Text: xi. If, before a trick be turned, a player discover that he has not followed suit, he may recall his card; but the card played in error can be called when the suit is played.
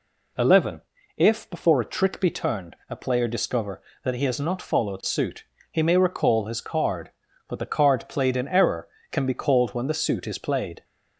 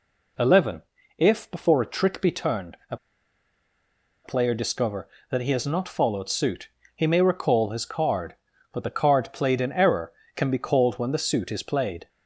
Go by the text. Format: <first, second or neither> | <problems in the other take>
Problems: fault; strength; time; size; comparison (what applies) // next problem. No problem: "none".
first | pauses between "a" and "player"; strong; at 2.9 s; 1.2 s long